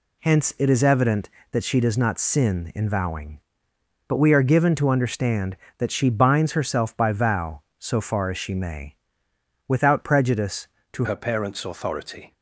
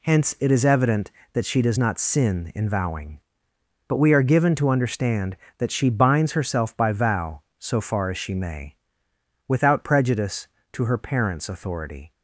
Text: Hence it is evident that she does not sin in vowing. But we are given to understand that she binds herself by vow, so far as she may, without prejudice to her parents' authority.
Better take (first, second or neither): second